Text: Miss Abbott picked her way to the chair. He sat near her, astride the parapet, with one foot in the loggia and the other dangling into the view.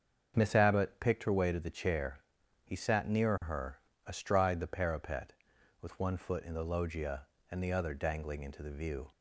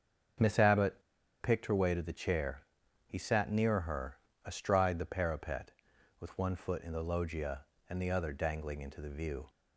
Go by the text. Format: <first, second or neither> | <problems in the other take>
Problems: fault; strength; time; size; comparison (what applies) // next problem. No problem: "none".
first | starts louder than the rest; until 1.8 s; 7 dB; also in the first // pauses between "Abbott" and "picked"; at 1.0 s; 0.39 s long